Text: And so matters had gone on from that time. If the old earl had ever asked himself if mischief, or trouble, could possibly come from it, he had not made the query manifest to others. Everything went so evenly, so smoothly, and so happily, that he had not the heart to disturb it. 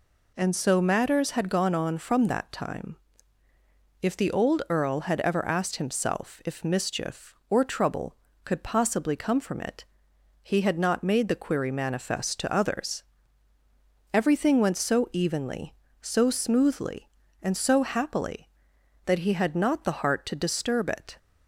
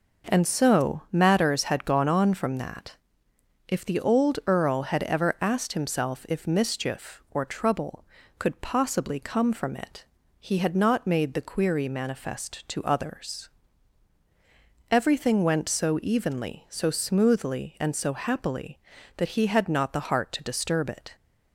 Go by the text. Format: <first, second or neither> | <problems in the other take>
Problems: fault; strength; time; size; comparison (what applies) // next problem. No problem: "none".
first | skips "time"; at 3.3 s